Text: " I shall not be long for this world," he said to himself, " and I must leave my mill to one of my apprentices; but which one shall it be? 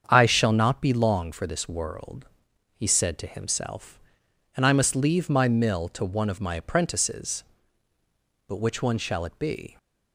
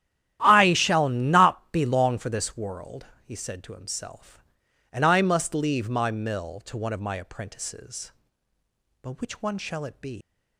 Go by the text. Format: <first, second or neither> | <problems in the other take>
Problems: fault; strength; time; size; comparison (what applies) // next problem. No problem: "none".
first | starts louder than the rest; strong; until 1.4 s; 11.5 dB; strong in the first // leaves "be" unfinished; at 10.2 s; 180 ms